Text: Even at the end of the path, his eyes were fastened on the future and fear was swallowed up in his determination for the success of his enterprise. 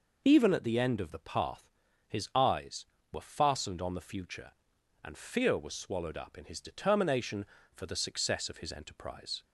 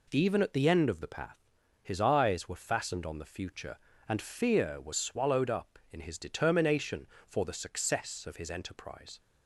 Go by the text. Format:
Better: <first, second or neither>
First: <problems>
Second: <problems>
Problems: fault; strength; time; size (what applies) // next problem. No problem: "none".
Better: neither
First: none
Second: none